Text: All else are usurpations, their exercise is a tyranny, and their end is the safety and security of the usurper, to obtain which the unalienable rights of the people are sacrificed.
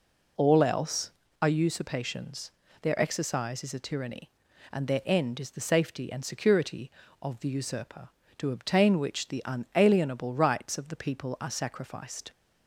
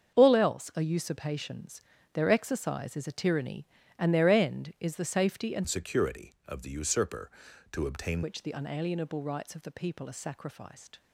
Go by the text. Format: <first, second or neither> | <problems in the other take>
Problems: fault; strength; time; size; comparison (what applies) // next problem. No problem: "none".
first | starts louder than the rest; until 1.2 s; 7 dB // changes voice from "security" to "obtain"; from 5.6 to 8.2 s; 2.6 s long